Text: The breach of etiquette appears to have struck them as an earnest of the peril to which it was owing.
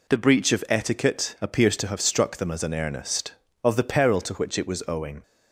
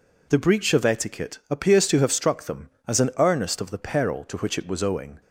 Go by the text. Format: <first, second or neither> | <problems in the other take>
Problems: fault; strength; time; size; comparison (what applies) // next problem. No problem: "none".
neither | none